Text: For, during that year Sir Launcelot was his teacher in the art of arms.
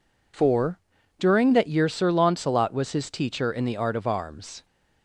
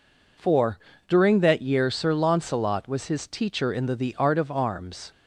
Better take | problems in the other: first | says "the" twice; at 3.9 s

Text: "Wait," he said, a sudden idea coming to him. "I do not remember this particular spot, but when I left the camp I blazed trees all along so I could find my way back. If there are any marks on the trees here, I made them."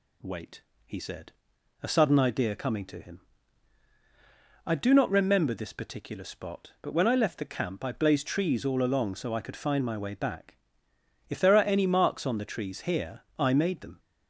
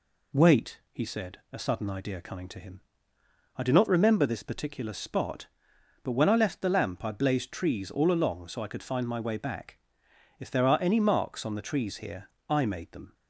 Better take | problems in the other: first | says "lamp" for "camp"; at 6.6 s

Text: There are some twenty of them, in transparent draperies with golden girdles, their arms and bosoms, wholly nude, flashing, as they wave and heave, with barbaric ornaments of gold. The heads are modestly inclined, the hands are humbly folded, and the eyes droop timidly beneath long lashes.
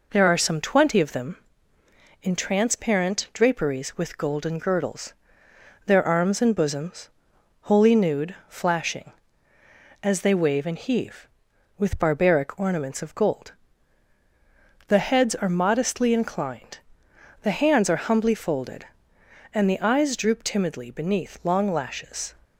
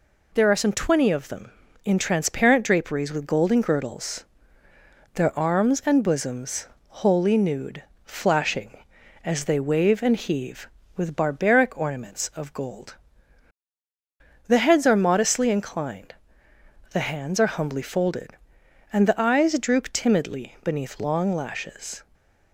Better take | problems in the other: neither | none

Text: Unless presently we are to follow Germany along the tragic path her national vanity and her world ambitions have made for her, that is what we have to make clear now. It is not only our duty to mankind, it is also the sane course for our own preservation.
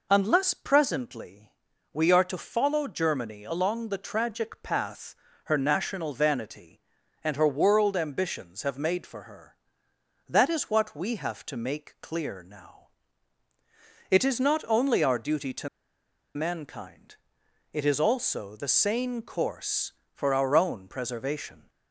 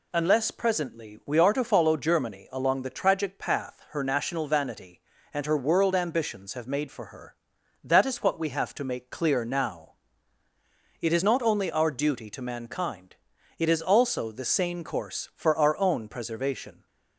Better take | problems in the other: second | pauses between "presently" and "we"; at 1.4 s; 0.42 s long // pauses between "path" and "her"; slight; at 5.1 s; 0.28 s long // pauses between "to" and "mankind"; noticeable; at 15.6 s; 0.67 s long

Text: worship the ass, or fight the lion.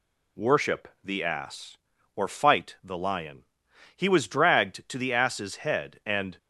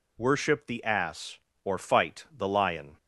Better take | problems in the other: second | pauses between "worship" and "the"; slight; at 0.8 s; 0.16 s long // goes on to say "He was dragged to the ass's head and"; strong; from 3.9 s on; 2.4 s long

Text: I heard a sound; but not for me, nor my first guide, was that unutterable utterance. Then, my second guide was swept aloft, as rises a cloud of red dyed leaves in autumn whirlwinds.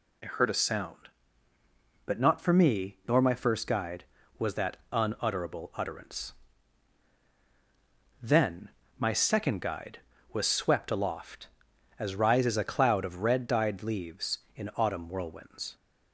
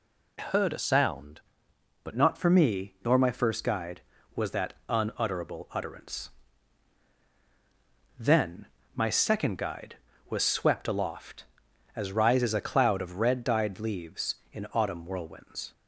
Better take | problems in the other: first | changes voice from "heard" to "but"; from 0.3 to 2.1 s; 1.8 s long

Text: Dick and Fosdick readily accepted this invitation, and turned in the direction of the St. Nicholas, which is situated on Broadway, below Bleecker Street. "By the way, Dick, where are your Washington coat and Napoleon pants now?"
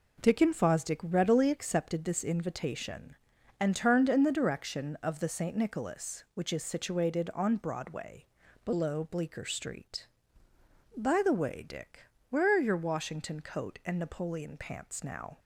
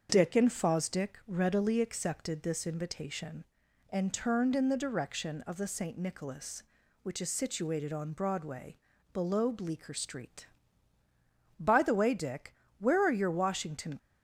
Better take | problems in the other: first | starts louder than the rest; until 1.1 s; 6.5 dB // stops before "coat and Napoleon pants now"; at 13.9 s

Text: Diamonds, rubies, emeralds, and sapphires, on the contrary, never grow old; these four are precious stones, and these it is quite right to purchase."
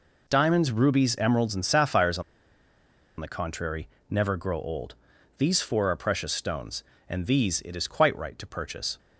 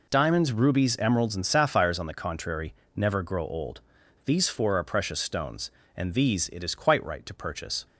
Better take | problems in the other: second | pauses between "on" and "the"; noticeable; at 2.2 s; 0.96 s long

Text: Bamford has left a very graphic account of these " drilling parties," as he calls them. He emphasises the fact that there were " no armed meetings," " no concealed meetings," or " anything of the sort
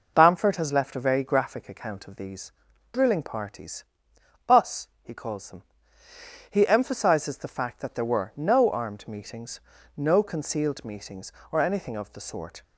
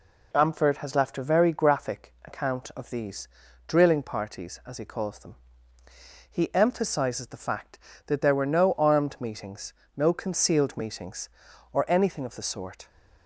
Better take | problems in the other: second | says "us" for "as"; at 4.4 s

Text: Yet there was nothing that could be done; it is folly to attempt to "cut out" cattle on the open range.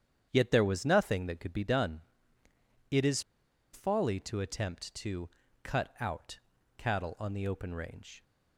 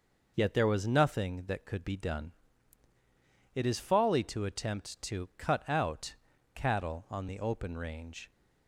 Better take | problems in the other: second | starts louder than the rest; strong; until 1.3 s; 9 dB // pauses between "is" and "folly"; noticeable; at 3.2 s; 0.50 s long // pauses between "to" and "cut"; slight; at 5.2 s; 0.34 s long // pauses between "out" and "cattle"; at 6.3 s; 0.38 s long; also in the second

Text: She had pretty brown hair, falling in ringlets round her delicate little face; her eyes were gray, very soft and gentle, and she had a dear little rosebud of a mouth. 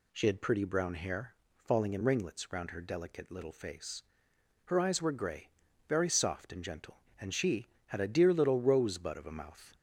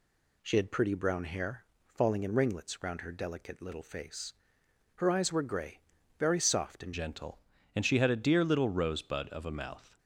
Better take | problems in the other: first | changes voice at "gentle"; from 6.9 s on; 3.0 s long

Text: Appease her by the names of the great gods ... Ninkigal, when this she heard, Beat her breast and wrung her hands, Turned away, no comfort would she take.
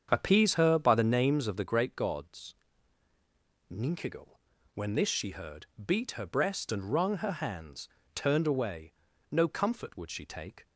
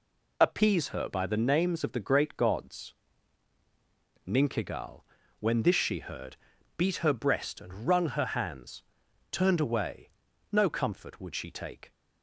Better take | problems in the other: second | starts louder than the rest; strong; until 1.2 s; 7.5 dB

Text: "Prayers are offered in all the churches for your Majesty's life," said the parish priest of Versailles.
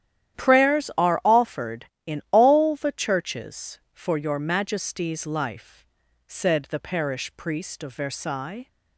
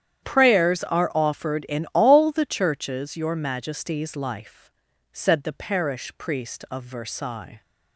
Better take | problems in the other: first | starts louder than the rest; strong; until 1.2 s; 9.5 dB; strong in the first // skips "for"; at 3.1 s

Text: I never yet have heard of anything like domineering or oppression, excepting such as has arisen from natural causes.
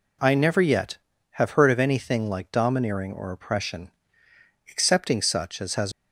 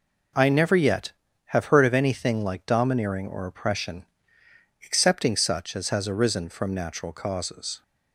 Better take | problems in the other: second | stops before "arisen from natural causes"; at 5.9 s

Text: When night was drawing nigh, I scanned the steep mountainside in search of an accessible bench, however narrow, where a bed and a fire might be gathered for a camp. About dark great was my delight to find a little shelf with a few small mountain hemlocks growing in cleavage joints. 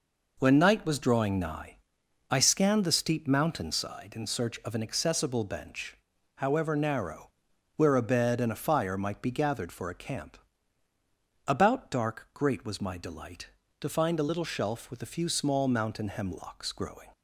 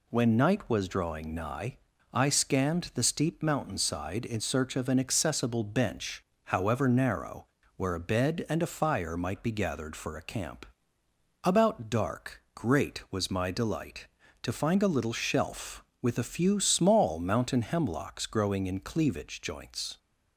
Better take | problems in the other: second | stops before "in cleavage joints"; at 17.1 s

